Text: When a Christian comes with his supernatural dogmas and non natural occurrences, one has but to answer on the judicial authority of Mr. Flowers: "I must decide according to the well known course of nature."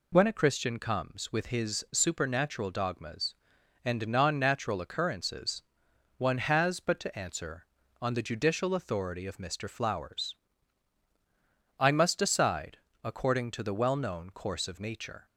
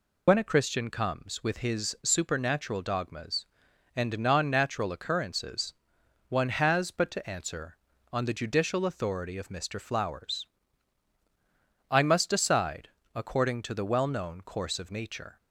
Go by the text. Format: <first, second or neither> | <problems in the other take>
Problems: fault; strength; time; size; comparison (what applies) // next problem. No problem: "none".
first | loses the start of "When"; at 0.2 s; 40 ms // pauses between "decide" and "according"; slight; at 12.8 s; 0.26 s long; slight in the first